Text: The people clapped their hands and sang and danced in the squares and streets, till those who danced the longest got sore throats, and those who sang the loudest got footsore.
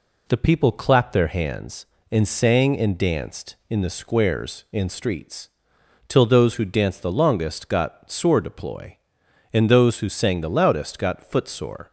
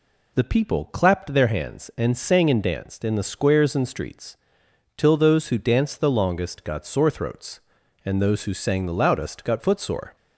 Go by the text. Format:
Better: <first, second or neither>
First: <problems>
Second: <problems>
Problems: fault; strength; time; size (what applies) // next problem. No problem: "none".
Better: second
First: says "deploy" for "throats"; at 8.4 s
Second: none